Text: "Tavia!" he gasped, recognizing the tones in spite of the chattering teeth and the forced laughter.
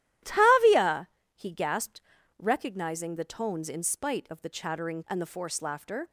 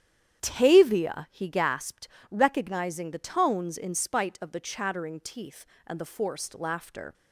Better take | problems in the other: second | starts louder than the rest; strong; until 1.5 s; 13 dB; strong in the second // skips "teeth"; at 5.0 s

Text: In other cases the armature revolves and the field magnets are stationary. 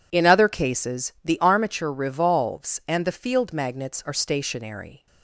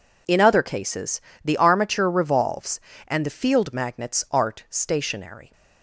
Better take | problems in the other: first | pauses between "cases" and "the"; slight; at 1.1 s; 0.24 s long // says "art" for "are"; at 4.2 s

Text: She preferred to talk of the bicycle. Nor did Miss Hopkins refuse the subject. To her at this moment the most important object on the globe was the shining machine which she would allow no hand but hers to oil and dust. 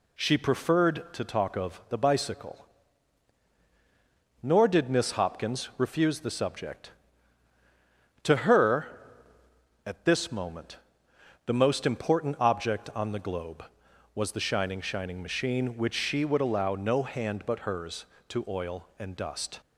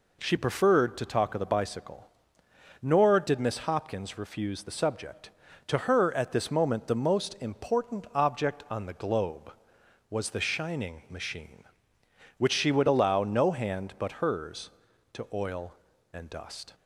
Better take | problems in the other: second | pauses between "moment" and "the"; noticeable; at 10.7 s; 0.68 s long // says "shining" twice; at 14.8 s

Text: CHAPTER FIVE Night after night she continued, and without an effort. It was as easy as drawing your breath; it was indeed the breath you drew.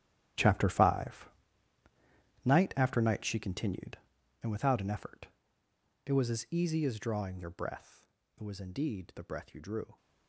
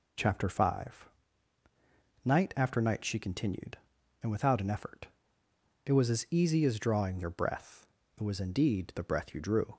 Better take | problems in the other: second | gets quieter; strong; throughout; 14.5 dB // pauses between "FIVE" and "Night"; at 1.3 s; 1.1 s long; also in the second

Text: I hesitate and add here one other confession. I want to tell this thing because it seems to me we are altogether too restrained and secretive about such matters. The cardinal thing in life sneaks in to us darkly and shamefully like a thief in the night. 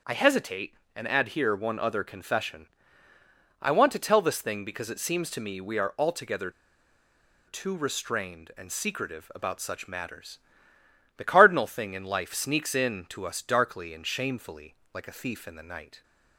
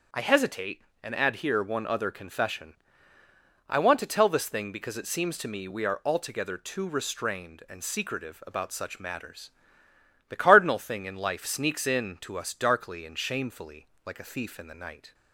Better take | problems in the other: second | starts louder than the rest; until 1.2 s; 7 dB; also in the second // pauses between "altogether" and "too"; noticeable; at 6.4 s; 0.97 s long // pauses between "shamefully" and "like"; slight; at 14.7 s; 0.18 s long; slight in the second

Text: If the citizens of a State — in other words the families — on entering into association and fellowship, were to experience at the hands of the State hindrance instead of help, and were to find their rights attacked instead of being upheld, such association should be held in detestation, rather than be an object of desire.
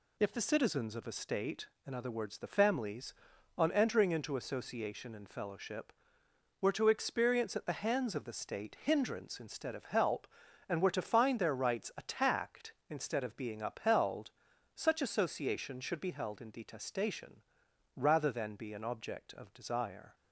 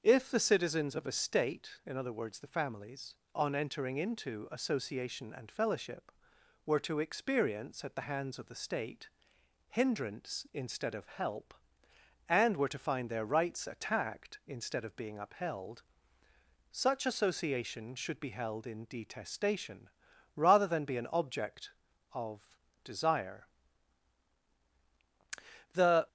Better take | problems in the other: first | starts louder than the rest; until 1.0 s; 6.5 dB // pauses between "State" and "hindrance"; noticeable; at 9.0 s; 0.62 s long // pauses between "of" and "desire"; slight; at 22.5 s; 0.30 s long // goes on to say "The"; slight; from 25.7 s on; 0.34 s long

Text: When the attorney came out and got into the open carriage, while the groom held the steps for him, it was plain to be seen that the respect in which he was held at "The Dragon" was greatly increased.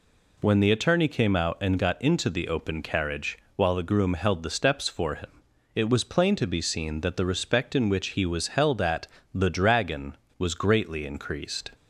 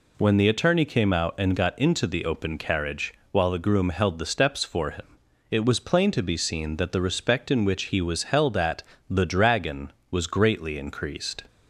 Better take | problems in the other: neither | pauses between "at" and "The"; slight; the same in both

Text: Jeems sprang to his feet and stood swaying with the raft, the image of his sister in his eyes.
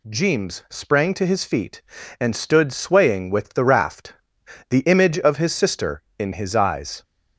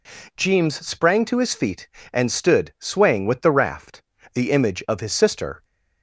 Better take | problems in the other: first | stops before "in his eyes"; at 5.6 s

